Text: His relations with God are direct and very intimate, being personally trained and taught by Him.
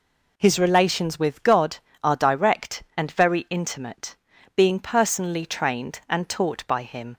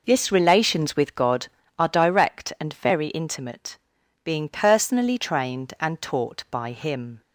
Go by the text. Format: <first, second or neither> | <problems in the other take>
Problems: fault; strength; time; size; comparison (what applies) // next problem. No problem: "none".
first | says "This" for "His"; at 0.0 s